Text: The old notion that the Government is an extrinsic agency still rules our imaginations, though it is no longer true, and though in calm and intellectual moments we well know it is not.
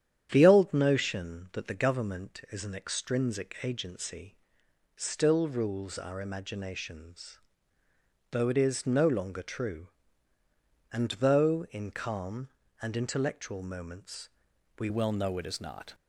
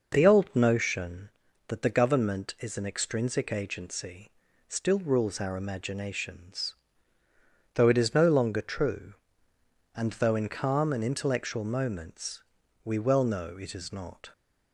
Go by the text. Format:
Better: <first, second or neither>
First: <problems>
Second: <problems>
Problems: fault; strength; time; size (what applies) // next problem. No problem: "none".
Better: second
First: starts louder than the rest; strong; until 1.3 s; 9.5 dB // pauses between "agency" and "still"; noticeable; at 4.3 s; 0.58 s long // pauses between "moments" and "we"; noticeable; at 14.2 s; 0.50 s long // changes voice at "well"; from 14.8 s on; 1.1 s long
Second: pauses between "agency" and "still"; at 4.2 s; 0.38 s long // pauses between "moments" and "we"; at 12.4 s; 0.42 s long